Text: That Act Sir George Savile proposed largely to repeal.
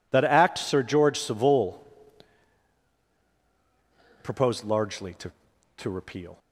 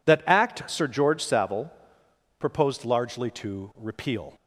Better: second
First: pauses between "Savile" and "proposed"; strong; at 1.8 s; 2.3 s long // says "to" twice; at 5.7 s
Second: pauses between "Savile" and "proposed"; noticeable; at 1.7 s; 0.70 s long

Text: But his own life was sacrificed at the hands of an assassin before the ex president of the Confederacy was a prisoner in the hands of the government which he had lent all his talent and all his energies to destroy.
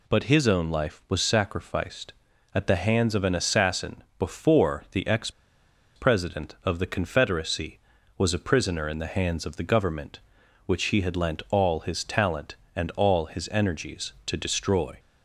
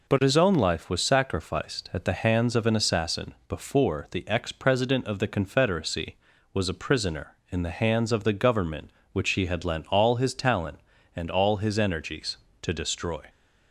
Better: second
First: pauses between "ex" and "president"; noticeable; at 5.2 s; 0.66 s long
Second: none

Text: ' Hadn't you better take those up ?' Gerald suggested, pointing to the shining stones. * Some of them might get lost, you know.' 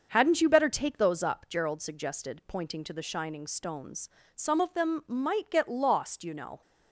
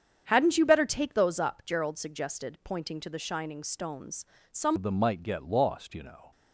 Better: first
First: starts louder than the rest; until 1.1 s; 6.5 dB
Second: starts louder than the rest; strong; until 1.2 s; 8 dB // changes voice at "of"; from 4.7 s on; 1.6 s long

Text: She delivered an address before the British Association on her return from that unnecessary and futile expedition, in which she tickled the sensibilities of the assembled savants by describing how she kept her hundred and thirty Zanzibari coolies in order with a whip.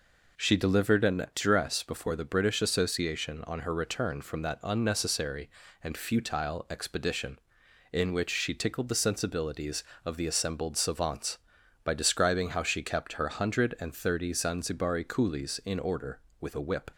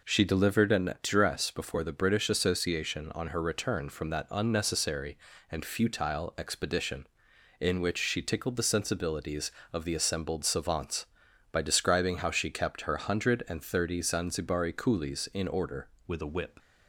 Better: first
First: none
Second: changes voice at "with"; from 16.0 s on; 0.5 s long

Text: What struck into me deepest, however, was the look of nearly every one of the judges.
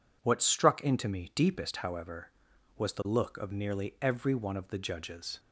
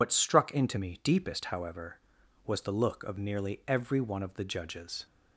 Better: first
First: none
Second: loses the start of "What"; at 0.0 s; 95 ms

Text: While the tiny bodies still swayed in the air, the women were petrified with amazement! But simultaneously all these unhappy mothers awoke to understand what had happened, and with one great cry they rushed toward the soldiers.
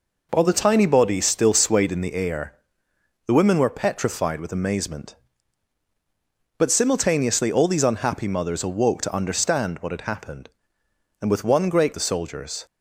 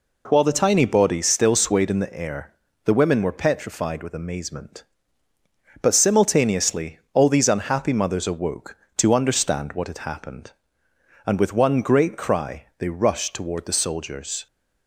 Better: second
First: skips "cry they rushed toward"; at 11.9 s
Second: none

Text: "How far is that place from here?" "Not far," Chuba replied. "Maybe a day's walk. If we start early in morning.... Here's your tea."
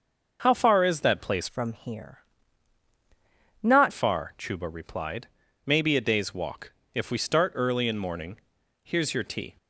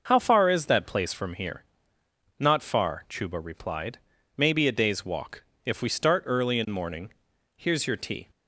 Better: second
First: changes voice from "from" to "Not"; from 1.4 to 3.9 s; 2.5 s long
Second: none

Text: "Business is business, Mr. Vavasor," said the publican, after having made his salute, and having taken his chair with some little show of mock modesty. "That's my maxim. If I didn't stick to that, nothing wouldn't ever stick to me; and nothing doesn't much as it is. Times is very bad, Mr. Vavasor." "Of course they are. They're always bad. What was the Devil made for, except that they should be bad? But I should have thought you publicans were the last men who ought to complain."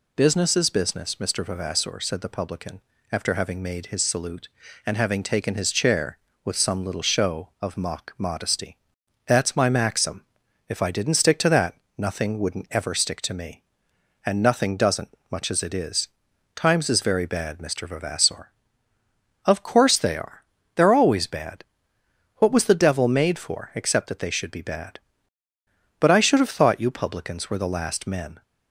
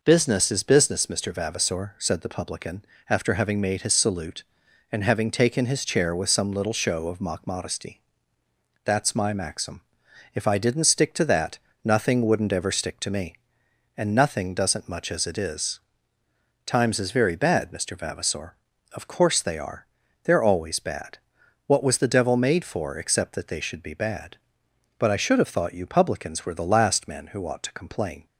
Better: second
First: stops before "who ought to complain"; at 28.4 s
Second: none

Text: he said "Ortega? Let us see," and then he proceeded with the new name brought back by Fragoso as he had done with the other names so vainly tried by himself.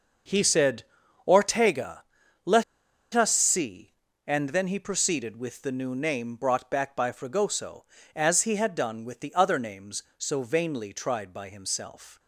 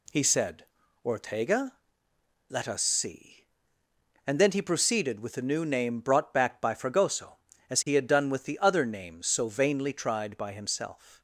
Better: second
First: starts louder than the rest; noticeable; until 1.6 s; 6 dB // pauses between "said" and "Ortega"; at 0.8 s; 0.42 s long // pauses between "Let" and "us"; noticeable; at 2.6 s; 0.51 s long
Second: pauses between "said" and "Ortega"; at 0.6 s; 0.40 s long

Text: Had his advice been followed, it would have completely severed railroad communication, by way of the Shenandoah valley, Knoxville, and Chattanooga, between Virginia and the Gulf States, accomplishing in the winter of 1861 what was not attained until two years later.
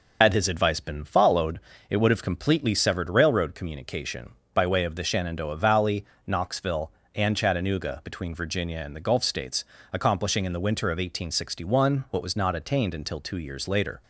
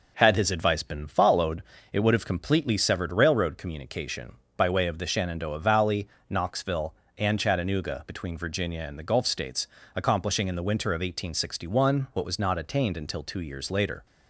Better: second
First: loses the start of "Had"; at 0.2 s; 80 ms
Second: none

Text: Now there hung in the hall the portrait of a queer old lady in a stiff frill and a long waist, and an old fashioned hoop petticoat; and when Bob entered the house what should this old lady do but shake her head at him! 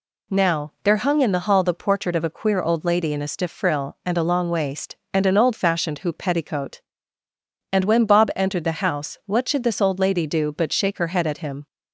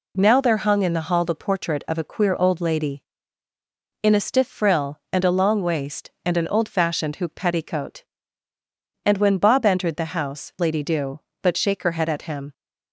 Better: first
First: none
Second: skips "what should this old"; at 10.5 s

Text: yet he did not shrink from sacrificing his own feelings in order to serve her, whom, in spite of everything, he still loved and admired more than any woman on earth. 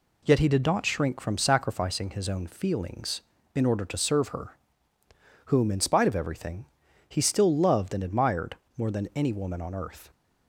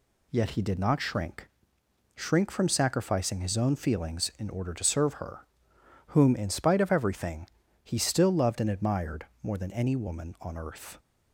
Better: first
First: pauses between "admired" and "more"; slight; at 8.5 s; 0.22 s long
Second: says "shrink" twice; at 2.1 s // pauses between "admired" and "more"; slight; at 9.2 s; 0.16 s long

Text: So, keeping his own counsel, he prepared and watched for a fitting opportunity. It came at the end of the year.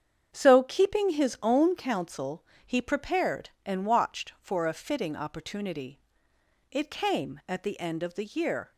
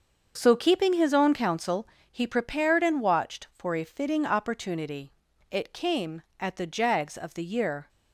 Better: first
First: starts louder than the rest; strong; until 1.3 s; 8 dB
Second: starts louder than the rest; until 1.3 s; 6.5 dB // says "jags" for "end"; at 6.6 s

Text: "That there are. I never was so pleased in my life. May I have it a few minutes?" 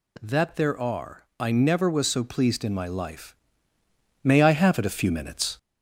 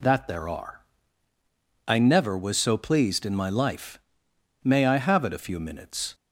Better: second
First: gets louder; slight; throughout; 3 dB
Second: none

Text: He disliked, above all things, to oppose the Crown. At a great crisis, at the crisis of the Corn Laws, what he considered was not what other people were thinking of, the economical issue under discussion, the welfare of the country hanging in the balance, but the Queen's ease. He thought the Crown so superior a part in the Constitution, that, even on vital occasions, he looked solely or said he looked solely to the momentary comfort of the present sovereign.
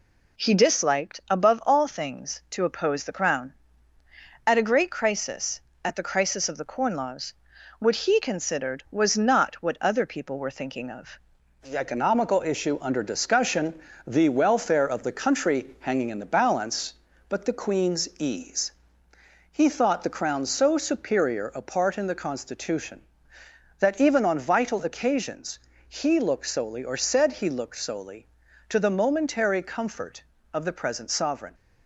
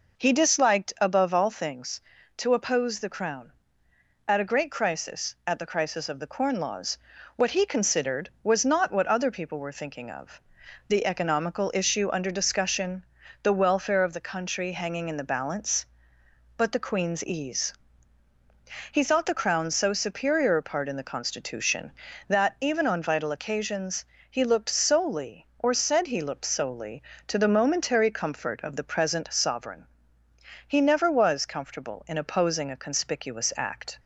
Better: first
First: none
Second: goes on to say "He never was comfortable in opposing a conspicuous act"; strong; from 30.6 s on; 3.3 s long

